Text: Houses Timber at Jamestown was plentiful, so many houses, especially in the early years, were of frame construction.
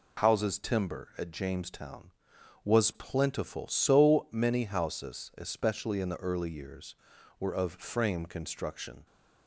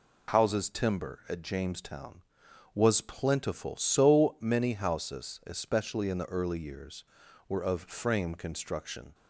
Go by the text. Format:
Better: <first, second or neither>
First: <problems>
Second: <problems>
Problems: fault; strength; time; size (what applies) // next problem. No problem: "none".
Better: neither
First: none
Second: none